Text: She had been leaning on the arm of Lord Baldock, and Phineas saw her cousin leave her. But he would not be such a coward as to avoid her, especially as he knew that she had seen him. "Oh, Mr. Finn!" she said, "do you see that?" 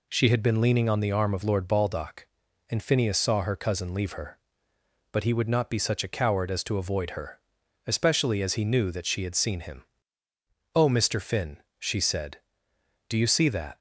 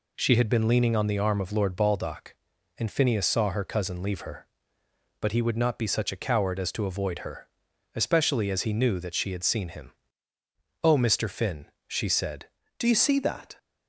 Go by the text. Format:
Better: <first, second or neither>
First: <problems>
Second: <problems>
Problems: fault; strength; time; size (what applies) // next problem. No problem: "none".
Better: first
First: none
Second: changes voice at "do"; from 12.7 s on; 0.8 s long